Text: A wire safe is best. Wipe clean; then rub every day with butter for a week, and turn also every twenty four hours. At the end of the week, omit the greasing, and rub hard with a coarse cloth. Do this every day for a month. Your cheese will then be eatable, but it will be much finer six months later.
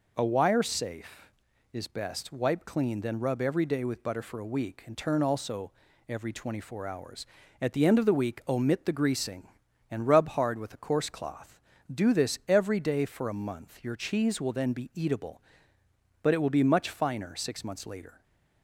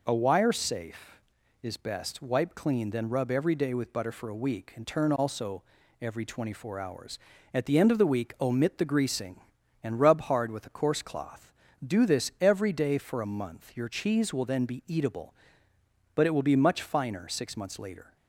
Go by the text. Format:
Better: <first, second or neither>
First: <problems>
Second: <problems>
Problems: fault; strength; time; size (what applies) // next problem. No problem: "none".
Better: neither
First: pauses between "also" and "every"; slight; at 5.7 s; 0.34 s long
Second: pauses between "also" and "every"; slight; at 5.6 s; 0.36 s long